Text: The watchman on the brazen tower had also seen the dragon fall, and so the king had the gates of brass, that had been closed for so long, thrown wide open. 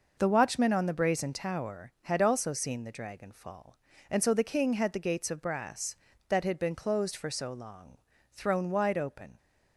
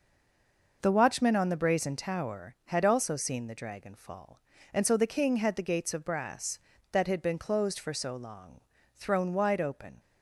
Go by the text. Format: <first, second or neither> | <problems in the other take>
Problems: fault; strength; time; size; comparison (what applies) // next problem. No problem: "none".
first | stays silent before the first word; slight; until 0.8 s; 0.8 s long